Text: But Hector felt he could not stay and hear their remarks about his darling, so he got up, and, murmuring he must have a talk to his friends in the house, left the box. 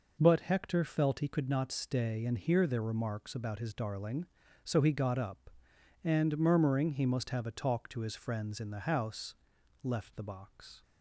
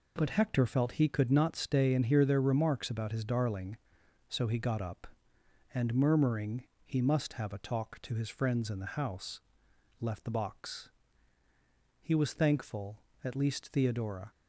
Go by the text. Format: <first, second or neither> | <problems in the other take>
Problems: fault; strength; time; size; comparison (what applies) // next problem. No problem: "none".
first | pauses between "murmuring" and "he"; slight; at 6.6 s; 0.24 s long // goes on to say "He was thankful at least Theodora"; strong; from 12.0 s on; 2.3 s long